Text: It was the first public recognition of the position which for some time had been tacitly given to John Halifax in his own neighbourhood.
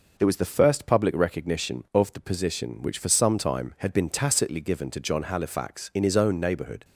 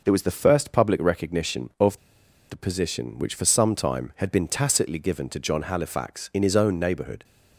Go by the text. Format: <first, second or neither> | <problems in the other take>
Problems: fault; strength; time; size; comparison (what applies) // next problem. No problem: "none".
first | pauses between "of" and "the"; noticeable; at 1.9 s; 0.51 s long